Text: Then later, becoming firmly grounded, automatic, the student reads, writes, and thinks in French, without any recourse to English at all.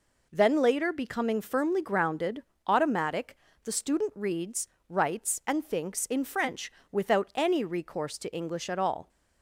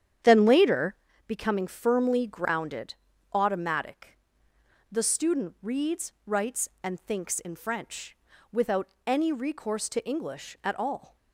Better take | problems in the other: first | starts louder than the rest; strong; until 1.1 s; 9 dB // pauses between "without" and "any"; slight; at 8.8 s; 0.18 s long

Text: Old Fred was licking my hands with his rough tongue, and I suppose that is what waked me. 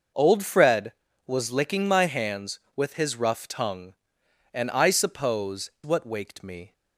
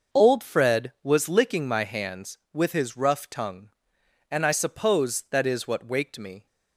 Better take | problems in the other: second | skips "that is"; at 5.7 s

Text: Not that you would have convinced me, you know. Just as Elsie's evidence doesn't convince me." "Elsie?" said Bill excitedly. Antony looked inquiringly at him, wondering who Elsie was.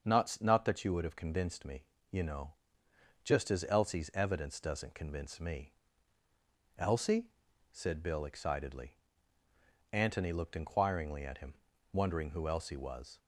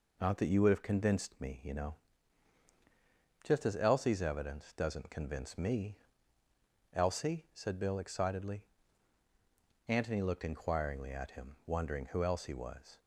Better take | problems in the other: second | starts louder than the rest; until 1.0 s; 6.5 dB // says "Not" twice; at 0.4 s

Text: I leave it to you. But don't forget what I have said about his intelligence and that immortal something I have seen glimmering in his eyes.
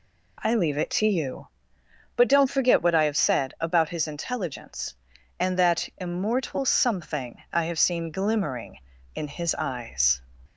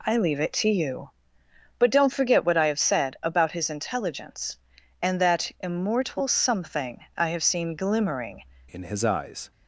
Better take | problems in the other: first | changes voice at "in"; from 8.7 s on; 0.8 s long

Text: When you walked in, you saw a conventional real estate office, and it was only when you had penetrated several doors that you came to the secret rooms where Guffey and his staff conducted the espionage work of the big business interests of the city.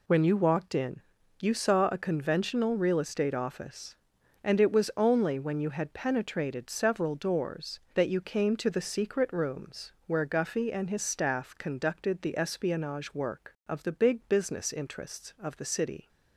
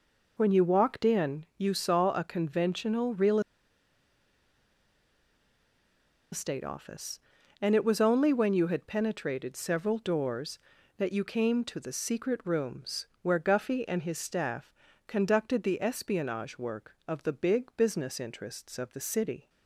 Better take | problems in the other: first | pauses between "real" and "estate"; strong; at 3.3 s; 2.9 s long // pauses between "rooms" and "where"; slight; at 13.0 s; 0.18 s long // pauses between "staff" and "conducted"; slight; at 14.7 s; 0.34 s long

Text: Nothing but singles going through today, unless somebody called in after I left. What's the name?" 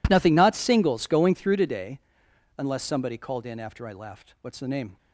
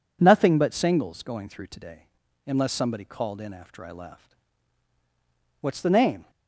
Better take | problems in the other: second | says "not" for "but"; at 0.3 s

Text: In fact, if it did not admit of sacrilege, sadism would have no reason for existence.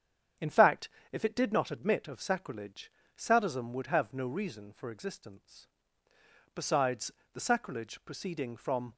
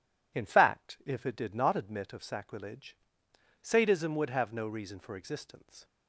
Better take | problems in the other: second | starts louder than the rest; strong; until 1.6 s; 8 dB // goes on to say "Besides the sacrilege proceeding from"; strong; from 6.5 s on; 2.4 s long

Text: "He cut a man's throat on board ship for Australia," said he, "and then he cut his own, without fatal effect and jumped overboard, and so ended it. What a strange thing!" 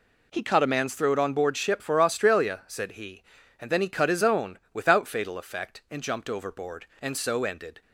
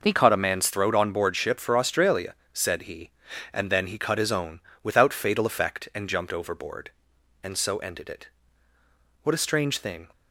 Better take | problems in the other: second | stops before "it What a strange thing"; at 7.8 s

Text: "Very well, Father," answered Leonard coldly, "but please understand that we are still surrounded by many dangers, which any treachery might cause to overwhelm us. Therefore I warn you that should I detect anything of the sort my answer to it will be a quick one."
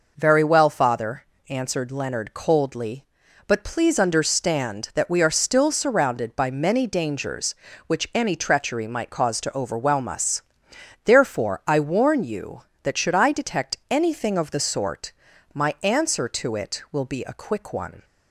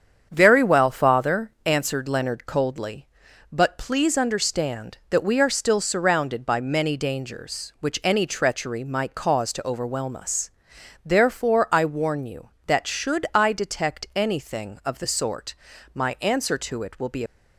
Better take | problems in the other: first | starts louder than the rest; strong; until 1.3 s; 8 dB // pauses between "sort" and "my"; at 15.5 s; 0.40 s long; also in the first // stops before "a quick one"; at 17.2 s

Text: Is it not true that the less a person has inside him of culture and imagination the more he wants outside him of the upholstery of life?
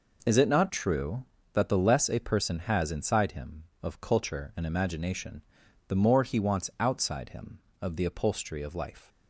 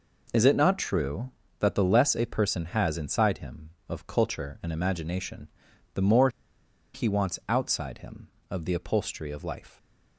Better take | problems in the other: first | pauses between "imagination" and "the"; noticeable; at 5.4 s; 0.46 s long; noticeable in the first // pauses between "more" and "he"; noticeable; at 6.2 s; 0.65 s long

